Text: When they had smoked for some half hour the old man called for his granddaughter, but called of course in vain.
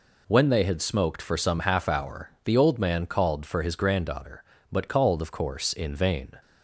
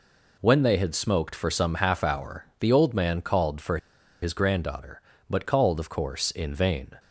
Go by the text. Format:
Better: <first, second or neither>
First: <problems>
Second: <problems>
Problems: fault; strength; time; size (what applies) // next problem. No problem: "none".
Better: first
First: pauses between "hour" and "the"; slight; at 2.2 s; 0.16 s long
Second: pauses between "hour" and "the"; slight; at 2.4 s; 0.16 s long // pauses between "for" and "his"; at 3.7 s; 0.44 s long